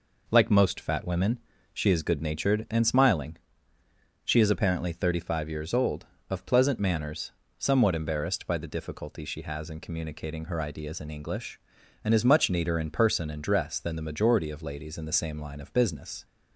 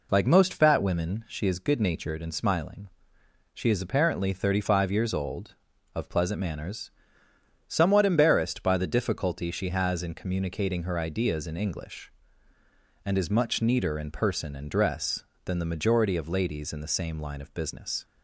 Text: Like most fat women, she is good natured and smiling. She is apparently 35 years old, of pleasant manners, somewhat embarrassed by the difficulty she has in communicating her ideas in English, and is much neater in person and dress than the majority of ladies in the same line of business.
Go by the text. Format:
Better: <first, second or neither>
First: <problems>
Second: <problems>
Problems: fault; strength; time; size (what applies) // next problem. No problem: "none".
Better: neither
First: none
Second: none